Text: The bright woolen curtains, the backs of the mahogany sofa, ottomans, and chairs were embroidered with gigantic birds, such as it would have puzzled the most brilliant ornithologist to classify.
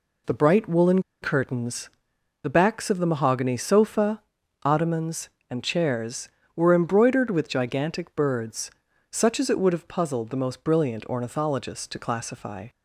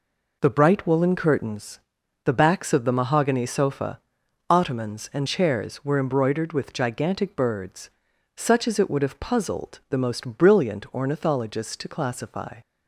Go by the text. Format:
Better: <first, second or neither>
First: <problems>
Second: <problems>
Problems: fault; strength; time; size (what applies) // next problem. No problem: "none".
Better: second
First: pauses between "woolen" and "curtains"; slight; at 1.0 s; 0.19 s long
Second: none